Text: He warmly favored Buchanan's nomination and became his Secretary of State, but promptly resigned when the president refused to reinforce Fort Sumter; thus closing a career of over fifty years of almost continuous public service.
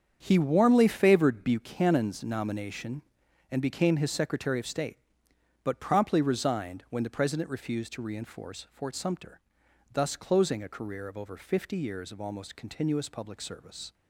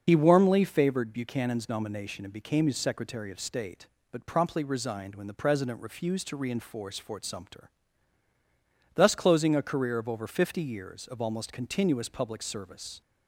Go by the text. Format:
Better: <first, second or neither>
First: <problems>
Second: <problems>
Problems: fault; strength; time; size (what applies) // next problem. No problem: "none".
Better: first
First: starts louder than the rest; strong; until 1.2 s; 7.5 dB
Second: loses the start of "He"; at 0.0 s; 55 ms // starts louder than the rest; noticeable; until 1.0 s; 6 dB